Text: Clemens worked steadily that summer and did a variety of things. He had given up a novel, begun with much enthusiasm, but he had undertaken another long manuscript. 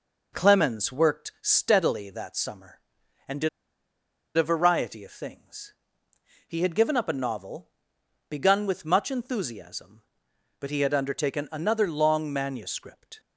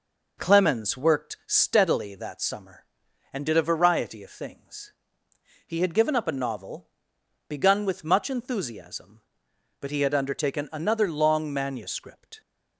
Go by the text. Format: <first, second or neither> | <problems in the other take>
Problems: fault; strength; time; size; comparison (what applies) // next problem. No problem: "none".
second | pauses between "did" and "a"; noticeable; at 3.4 s; 0.88 s long